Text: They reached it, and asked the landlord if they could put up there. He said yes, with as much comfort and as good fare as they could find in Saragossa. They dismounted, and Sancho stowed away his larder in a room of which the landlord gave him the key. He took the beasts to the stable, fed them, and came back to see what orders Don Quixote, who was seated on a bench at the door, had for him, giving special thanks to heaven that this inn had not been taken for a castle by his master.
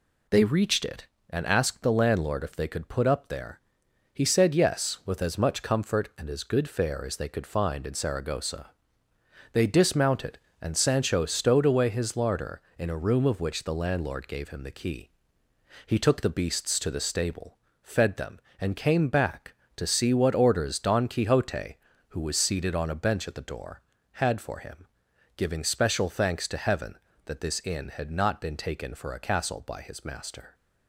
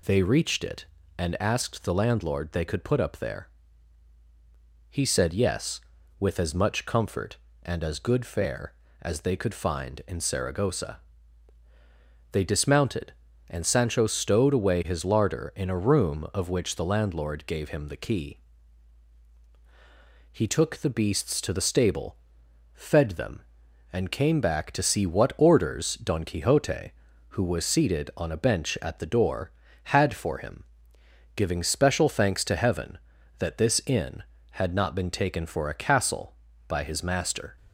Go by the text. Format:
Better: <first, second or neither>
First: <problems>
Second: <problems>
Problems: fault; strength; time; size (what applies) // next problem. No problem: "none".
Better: first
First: none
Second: skips "if"; at 2.5 s